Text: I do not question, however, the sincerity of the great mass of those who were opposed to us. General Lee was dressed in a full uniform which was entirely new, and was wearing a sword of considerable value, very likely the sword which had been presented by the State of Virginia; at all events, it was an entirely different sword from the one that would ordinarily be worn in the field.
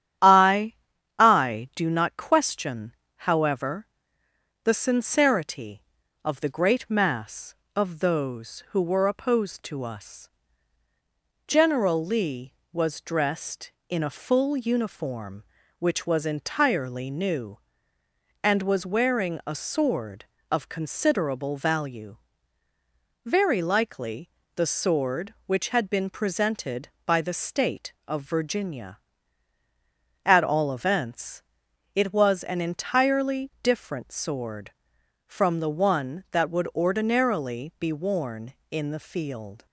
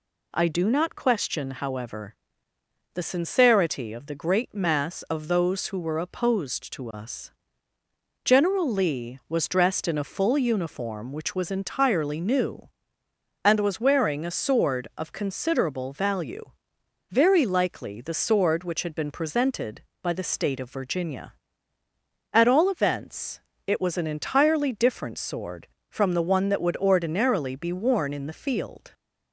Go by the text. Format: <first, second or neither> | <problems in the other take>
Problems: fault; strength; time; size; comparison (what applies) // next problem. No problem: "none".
second | starts louder than the rest; strong; until 1.6 s; 10 dB // says "I" twice; at 1.1 s // pauses between "likely" and "the"; slight; at 24.3 s; 0.24 s long